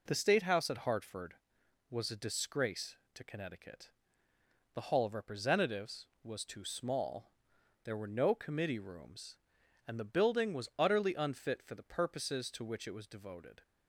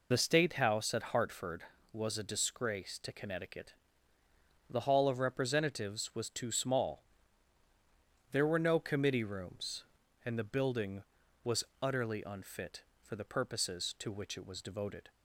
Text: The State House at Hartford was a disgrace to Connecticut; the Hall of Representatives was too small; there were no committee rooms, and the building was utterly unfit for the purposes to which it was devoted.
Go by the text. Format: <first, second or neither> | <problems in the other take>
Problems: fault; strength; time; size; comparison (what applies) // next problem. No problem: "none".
first | loses the start of "The"; at 0.1 s; 55 ms // pauses between "was" and "utterly"; slight; at 11.6 s; 0.18 s long